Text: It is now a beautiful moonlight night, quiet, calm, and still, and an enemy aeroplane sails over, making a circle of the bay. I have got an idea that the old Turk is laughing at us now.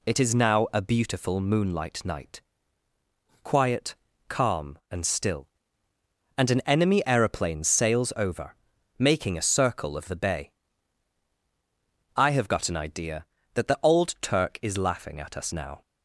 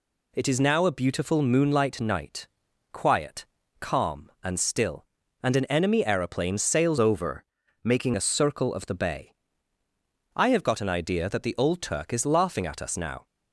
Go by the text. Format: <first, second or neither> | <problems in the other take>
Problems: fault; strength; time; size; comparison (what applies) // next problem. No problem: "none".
first | changes voice from "over" to "making"; from 6.9 to 8.1 s; 1.2 s long